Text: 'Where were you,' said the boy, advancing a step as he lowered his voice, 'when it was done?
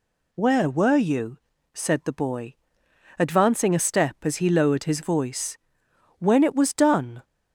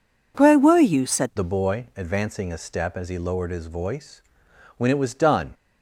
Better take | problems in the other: first | changes voice at "the"; from 1.3 s on; 4.2 s long

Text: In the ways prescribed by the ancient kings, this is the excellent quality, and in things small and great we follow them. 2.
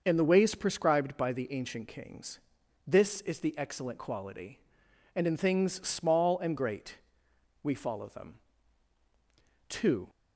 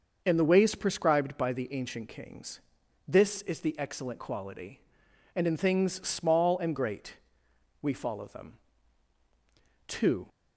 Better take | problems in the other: neither | starts louder than the rest; noticeable; the same in both // pauses between "great" and "we"; noticeable; the same in both

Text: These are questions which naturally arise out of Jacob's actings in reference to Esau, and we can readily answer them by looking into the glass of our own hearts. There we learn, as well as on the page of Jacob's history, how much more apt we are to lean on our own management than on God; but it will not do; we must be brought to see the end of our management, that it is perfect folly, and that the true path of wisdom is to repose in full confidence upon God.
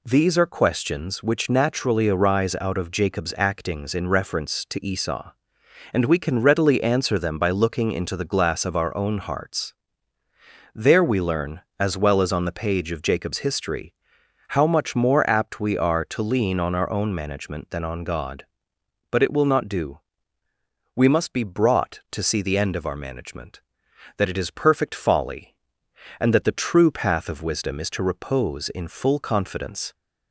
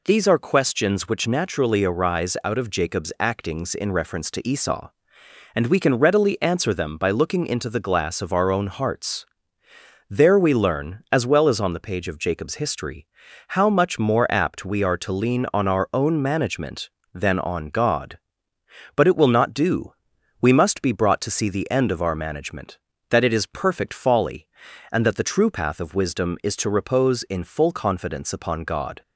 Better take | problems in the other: second | stops before "upon God"; at 29.9 s

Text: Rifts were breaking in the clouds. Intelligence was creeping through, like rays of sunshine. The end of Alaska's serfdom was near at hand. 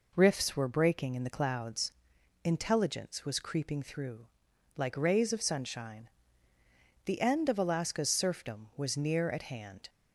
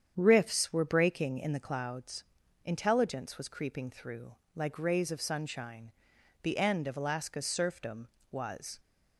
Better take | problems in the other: first | starts louder than the rest; strong; until 1.1 s; 8.5 dB // stops before "near at hand"; at 8.7 s

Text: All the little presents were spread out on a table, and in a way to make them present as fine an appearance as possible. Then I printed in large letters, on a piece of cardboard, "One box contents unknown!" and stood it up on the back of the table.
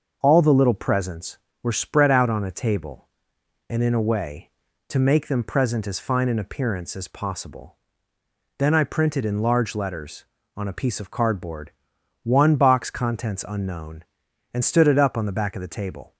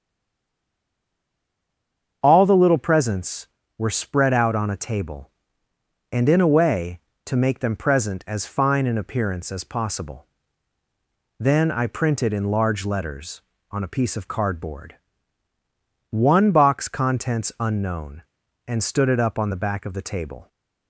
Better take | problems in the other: first | stays silent before the first word; until 2.2 s; 2.2 s long // starts louder than the rest; until 3.2 s; 7 dB; also in the first

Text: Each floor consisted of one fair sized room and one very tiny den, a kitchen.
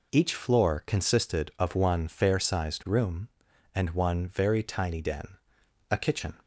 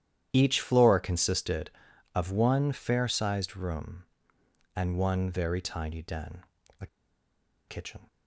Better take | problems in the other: first | starts louder than the rest; strong; until 1.3 s; 11 dB // pauses between "a" and "kitchen"; noticeable; at 6.8 s; 0.81 s long

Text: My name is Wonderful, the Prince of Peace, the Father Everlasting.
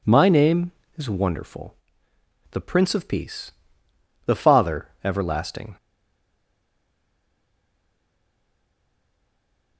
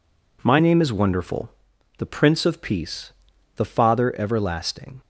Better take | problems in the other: second | pauses between "Father" and "Everlasting"; slight; at 4.8 s; 0.16 s long // stays silent after the last word; strong; from 5.7 s on; 4.0 s long

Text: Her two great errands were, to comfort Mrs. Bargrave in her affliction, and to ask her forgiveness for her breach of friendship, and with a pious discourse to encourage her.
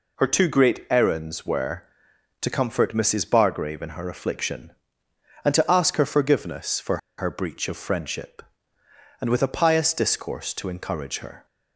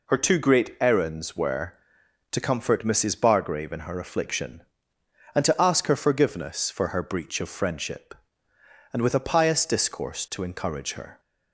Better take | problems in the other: second | pauses between "for" and "her"; slight; at 6.9 s; 0.21 s long

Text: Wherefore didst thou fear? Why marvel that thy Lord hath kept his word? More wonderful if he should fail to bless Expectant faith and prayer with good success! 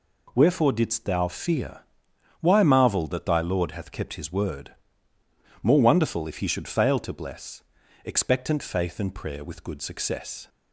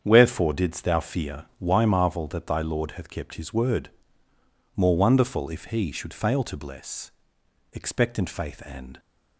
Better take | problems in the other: first | starts louder than the rest; strong; until 1.0 s; 8 dB // pauses between "bless" and "Expectant"; noticeable; at 7.1 s; 0.62 s long; also in the first // stops before "prayer with good success"; at 8.9 s

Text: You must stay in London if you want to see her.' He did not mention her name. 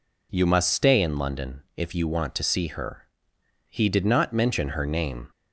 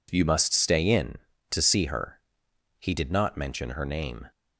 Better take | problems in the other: first | skips "London if you want"; at 1.3 s

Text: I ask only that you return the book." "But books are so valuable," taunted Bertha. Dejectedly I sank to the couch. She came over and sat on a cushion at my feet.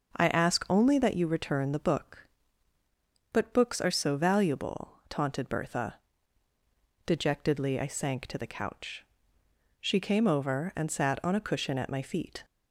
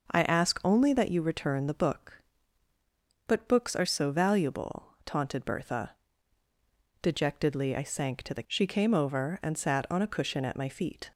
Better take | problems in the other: first | skips "couch"; at 8.4 s

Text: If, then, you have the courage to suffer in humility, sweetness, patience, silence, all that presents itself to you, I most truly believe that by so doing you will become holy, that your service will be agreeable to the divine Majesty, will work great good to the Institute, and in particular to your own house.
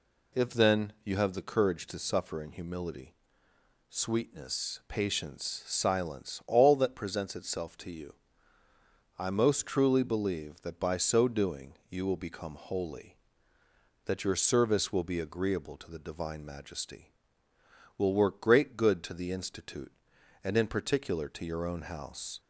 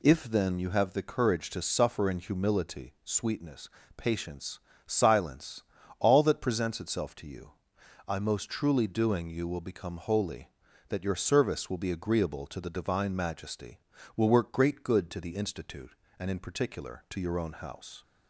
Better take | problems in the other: first | skips "believe that by so"; at 8.8 s

